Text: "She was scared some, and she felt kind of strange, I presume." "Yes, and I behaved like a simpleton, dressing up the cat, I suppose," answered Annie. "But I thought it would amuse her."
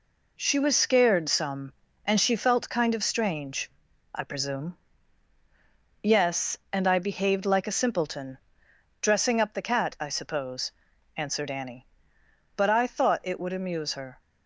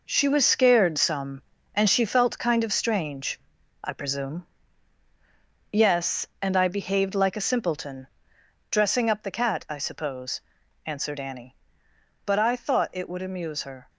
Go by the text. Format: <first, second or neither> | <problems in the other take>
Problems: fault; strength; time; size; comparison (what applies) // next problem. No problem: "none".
first | gets quieter; strong; throughout; 9 dB